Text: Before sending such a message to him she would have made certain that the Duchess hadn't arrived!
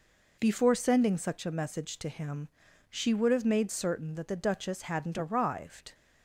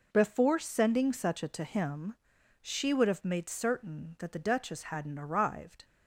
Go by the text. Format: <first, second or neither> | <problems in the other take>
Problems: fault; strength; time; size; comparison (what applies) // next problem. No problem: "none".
first | skips "message"; at 1.4 s // pauses between "him" and "she"; noticeable; at 2.1 s; 0.46 s long; also in the first